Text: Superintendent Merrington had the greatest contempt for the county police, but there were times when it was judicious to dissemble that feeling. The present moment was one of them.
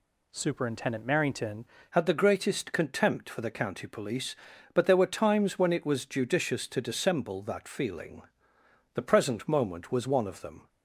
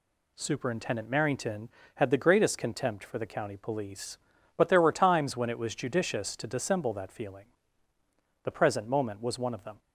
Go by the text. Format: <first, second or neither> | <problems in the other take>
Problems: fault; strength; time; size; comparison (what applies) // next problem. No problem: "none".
second | changes voice at "had"; from 1.9 s on; 8.7 s long